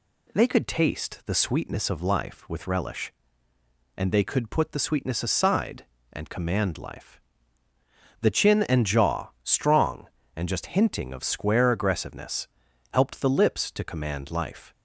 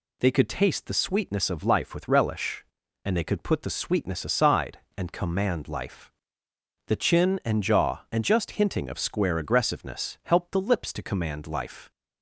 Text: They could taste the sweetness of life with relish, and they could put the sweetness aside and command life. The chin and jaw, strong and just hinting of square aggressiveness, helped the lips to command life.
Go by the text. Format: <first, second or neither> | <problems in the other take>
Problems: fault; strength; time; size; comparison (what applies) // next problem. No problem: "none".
first | skips "strong"; at 8.0 s